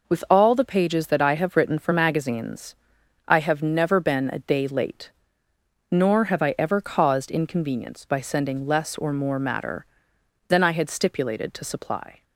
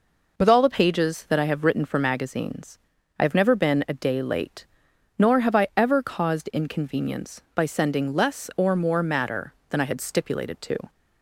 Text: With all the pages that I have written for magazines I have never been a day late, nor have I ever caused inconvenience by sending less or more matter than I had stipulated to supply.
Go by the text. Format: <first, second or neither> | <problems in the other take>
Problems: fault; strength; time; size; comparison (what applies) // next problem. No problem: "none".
first | pauses between "magazines" and "I"; at 2.7 s; 0.40 s long; noticeable in the first // stops before "supply"; at 10.8 s